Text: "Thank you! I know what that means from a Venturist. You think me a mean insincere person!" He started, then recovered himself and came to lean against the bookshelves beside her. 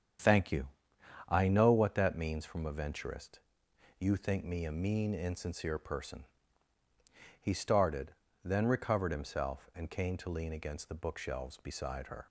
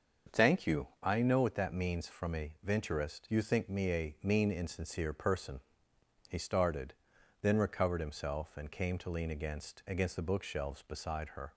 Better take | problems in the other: first | starts louder than the rest; until 1.4 s; 7 dB; strong in the first // says "against" twice; at 9.8 s

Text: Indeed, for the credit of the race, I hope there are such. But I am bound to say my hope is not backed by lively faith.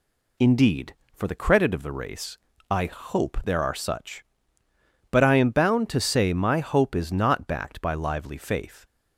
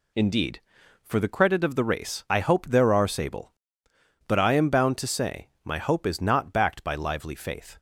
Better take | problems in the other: first | says "sable" for "such"; at 3.0 s // pauses between "say" and "my"; slight; at 5.4 s; 0.16 s long

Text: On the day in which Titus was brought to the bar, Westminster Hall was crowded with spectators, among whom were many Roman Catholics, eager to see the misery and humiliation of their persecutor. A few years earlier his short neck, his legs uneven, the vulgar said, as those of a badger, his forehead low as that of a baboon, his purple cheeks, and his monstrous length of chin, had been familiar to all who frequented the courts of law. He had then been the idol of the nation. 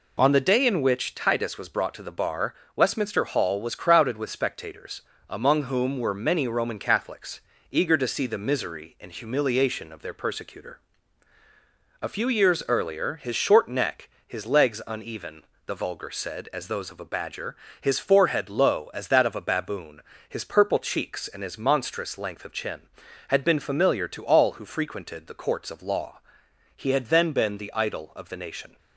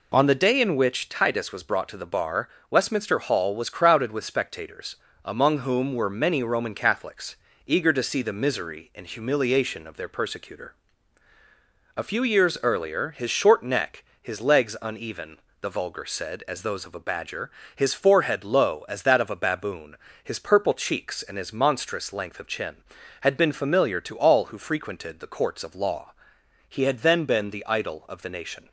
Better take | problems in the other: neither | none

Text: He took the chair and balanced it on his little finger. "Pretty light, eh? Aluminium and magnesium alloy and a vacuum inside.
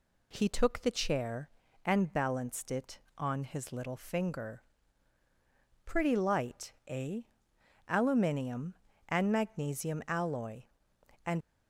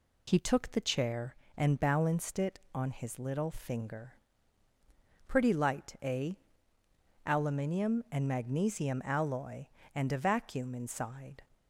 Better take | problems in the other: second | stops before "a vacuum inside"; at 11.4 s

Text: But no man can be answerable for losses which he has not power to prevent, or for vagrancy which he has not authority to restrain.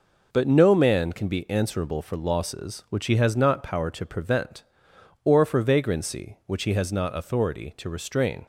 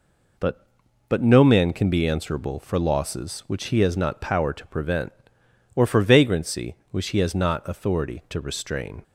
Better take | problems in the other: first | says "But" twice; at 1.0 s

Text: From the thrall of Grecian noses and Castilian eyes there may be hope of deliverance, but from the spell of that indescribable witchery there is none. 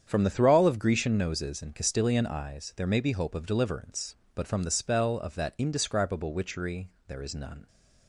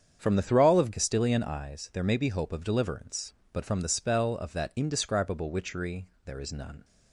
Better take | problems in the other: first | starts louder than the rest; strong; until 1.2 s; 8 dB; strong in the first // skips "Grecian noses and"; at 0.9 s // pauses between "witchery" and "there"; slight; at 6.0 s; 0.22 s long; slight in the first

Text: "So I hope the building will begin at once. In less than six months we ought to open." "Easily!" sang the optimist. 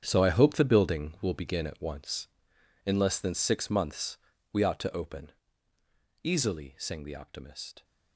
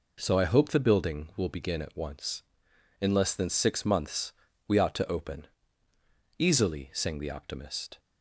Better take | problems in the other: second | gets quieter; strong; throughout; 13 dB // pauses between "months" and "we"; slight; at 4.1 s; 0.34 s long; slight in the second

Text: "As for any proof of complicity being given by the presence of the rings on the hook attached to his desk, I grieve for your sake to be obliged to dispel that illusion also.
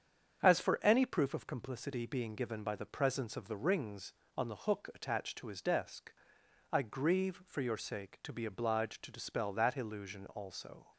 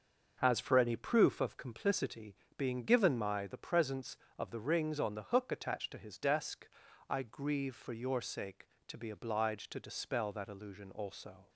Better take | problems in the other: first | starts louder than the rest; noticeable; until 1.4 s; 6 dB; strong in the first // pauses between "complicity" and "being"; slight; at 2.3 s; 0.20 s long // says "my" for "by"; at 3.1 s

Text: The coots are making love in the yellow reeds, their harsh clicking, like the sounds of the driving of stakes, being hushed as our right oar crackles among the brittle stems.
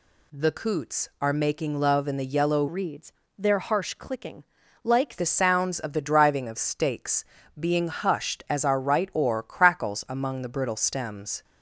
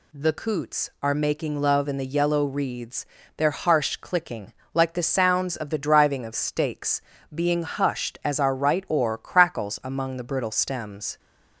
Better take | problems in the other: second | changes voice from "reeds" to "like"; from 2.6 to 5.1 s; 2.5 s long

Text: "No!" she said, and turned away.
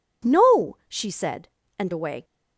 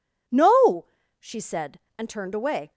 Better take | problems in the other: second | skips "turned"; at 1.9 s

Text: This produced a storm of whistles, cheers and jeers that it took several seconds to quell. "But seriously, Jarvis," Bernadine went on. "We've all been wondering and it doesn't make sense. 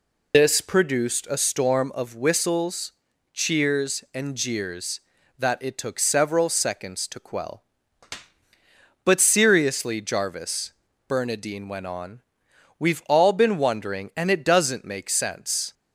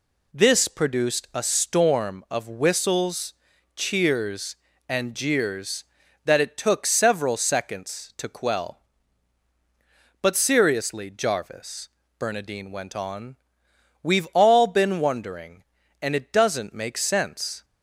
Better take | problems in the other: second | loses the start of "This"; at 0.3 s; 130 ms

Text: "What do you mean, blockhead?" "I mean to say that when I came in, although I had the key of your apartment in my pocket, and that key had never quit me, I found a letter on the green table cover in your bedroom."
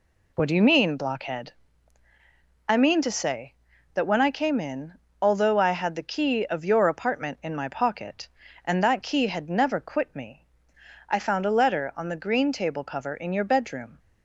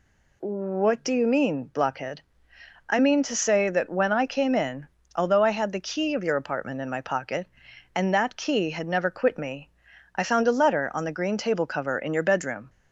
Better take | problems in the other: neither | none

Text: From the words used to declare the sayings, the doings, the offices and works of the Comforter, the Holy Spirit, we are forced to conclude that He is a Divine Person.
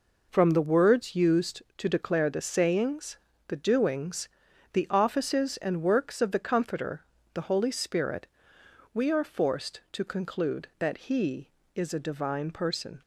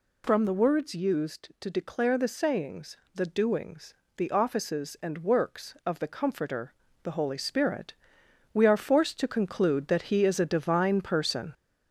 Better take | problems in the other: first | gets louder; throughout; 3.5 dB

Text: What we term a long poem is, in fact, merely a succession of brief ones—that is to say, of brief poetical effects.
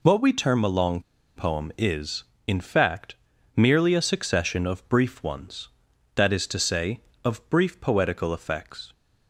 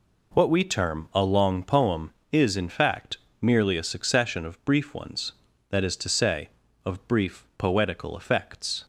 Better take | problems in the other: second | pauses between "long" and "poem"; slight; at 1.0 s; 0.35 s long

